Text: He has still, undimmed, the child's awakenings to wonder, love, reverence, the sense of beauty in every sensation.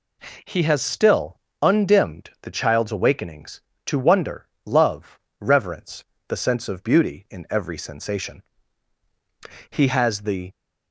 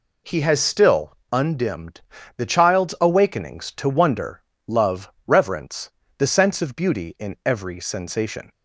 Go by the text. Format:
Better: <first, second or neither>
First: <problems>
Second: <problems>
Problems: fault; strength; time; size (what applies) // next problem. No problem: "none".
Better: second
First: goes on to say "He has the"; noticeable; from 9.6 s on; 0.82 s long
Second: none